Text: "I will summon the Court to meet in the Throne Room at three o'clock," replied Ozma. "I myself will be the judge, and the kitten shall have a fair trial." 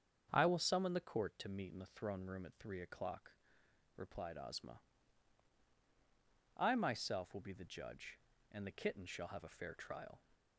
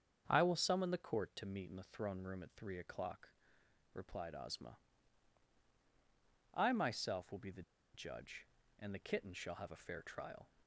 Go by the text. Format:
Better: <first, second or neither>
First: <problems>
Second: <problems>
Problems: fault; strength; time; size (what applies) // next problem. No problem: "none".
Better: first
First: starts louder than the rest; strong; until 1.3 s; 7 dB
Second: starts louder than the rest; strong; until 1.2 s; 7.5 dB // pauses between "the" and "judge"; slight; at 7.6 s; 0.32 s long